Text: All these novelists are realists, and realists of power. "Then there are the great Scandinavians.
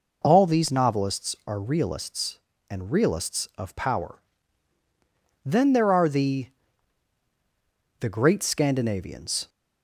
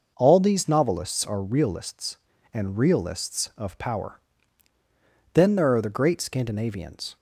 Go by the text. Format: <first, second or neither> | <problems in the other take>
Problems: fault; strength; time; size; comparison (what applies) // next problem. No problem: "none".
second | says "the" twice; at 7.9 s